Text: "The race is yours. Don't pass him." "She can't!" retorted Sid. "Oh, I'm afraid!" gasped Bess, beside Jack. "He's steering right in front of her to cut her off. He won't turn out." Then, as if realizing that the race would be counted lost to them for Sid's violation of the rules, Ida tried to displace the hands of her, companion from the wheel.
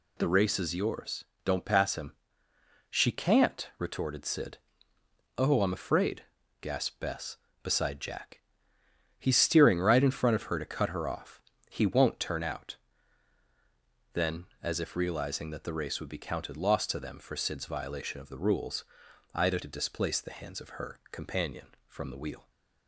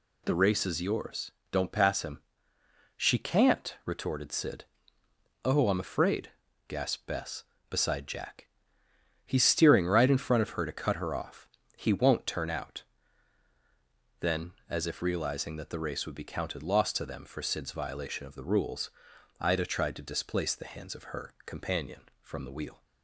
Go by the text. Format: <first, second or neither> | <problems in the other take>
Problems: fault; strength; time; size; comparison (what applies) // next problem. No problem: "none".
second | skips "tried"; at 19.6 s